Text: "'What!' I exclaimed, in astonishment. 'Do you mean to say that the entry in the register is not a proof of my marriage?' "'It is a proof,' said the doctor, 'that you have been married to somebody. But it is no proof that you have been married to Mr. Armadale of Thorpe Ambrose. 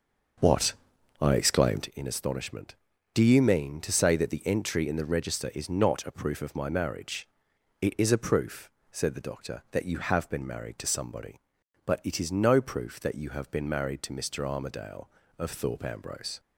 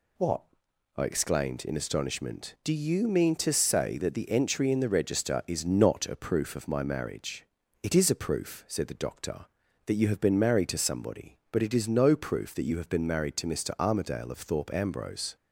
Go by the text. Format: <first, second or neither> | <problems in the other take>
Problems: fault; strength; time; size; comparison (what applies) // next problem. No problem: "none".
second | starts louder than the rest; noticeable; until 1.9 s; 6 dB